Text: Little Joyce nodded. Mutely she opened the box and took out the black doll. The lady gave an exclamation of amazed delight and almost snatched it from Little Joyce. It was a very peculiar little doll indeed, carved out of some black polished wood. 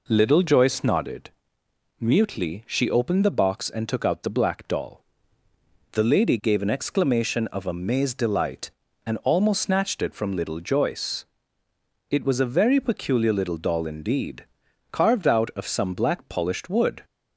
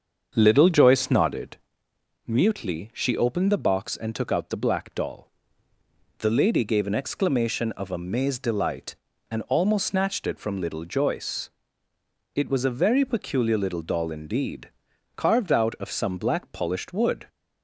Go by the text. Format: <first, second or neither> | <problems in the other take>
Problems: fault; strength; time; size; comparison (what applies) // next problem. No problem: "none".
first | starts louder than the rest; strong; until 1.7 s; 7 dB